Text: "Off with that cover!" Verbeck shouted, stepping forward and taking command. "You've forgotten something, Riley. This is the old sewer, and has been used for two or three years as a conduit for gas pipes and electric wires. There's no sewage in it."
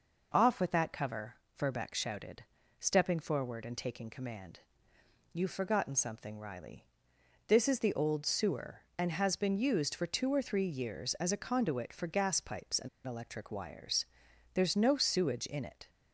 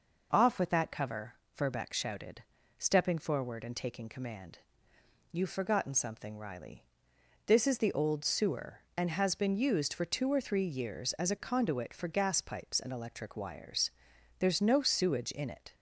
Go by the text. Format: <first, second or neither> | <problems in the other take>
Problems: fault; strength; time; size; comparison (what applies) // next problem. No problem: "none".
second | pauses between "and" and "electric"; slight; at 12.8 s; 0.17 s long